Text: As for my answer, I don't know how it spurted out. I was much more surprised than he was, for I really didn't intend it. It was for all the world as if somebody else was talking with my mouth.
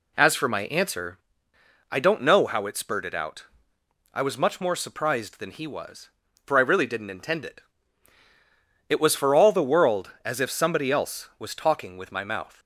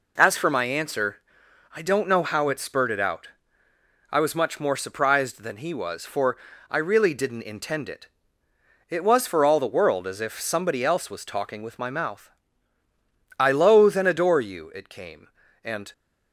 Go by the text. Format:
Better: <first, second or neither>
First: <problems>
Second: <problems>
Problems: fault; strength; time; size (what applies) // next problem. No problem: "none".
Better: first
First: none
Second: pauses between "for" and "I"; slight; at 6.3 s; 0.34 s long // goes on to say "I loathe and adore you it came and"; strong; from 13.3 s on; 2.5 s long